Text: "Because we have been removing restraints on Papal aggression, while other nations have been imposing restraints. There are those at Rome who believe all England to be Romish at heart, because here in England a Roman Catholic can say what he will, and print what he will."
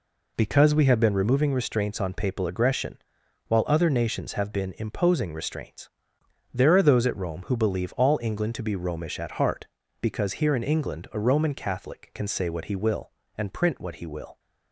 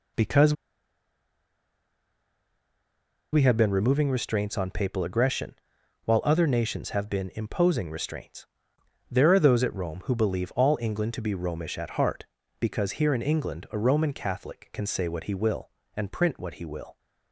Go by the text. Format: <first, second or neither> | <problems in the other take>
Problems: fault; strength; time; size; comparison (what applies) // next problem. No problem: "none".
first | pauses between "Because" and "we"; strong; at 0.5 s; 2.7 s long